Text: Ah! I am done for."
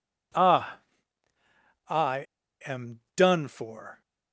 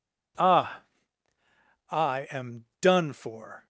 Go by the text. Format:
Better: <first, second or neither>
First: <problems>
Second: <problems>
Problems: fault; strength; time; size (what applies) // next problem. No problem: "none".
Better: second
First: pauses between "I" and "am"; at 2.2 s; 0.41 s long // pauses between "am" and "done"; slight; at 2.9 s; 0.16 s long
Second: pauses between "am" and "done"; slight; at 2.6 s; 0.16 s long